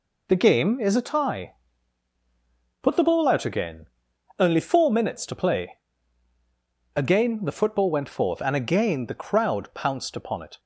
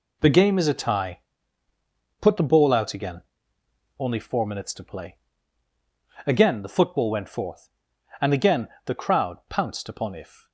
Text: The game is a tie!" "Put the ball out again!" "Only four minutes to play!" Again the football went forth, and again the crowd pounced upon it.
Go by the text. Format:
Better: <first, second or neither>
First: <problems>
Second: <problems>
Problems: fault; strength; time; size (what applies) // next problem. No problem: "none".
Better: first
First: none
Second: pauses between "again" and "the"; slight; at 8.6 s; 0.18 s long // says "if" for "it"; at 10.1 s